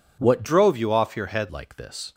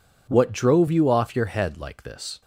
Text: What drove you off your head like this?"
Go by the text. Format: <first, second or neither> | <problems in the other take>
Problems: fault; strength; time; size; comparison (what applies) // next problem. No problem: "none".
second | changes voice from "drove" to "head"; from 0.4 to 1.4 s; 1.0 s long